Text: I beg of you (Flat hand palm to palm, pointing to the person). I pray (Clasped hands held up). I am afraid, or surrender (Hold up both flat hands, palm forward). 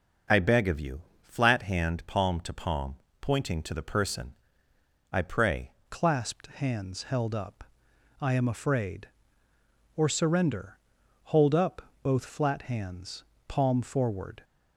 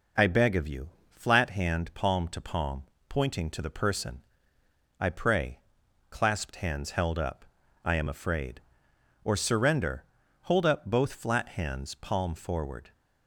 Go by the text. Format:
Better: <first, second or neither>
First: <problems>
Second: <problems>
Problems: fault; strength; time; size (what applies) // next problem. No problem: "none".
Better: second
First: starts louder than the rest; noticeable; until 1.5 s; 6 dB // changes voice at "Clasped"; from 5.8 s on; 8.6 s long // pauses between "up" and "both"; slight; at 11.8 s; 0.20 s long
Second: none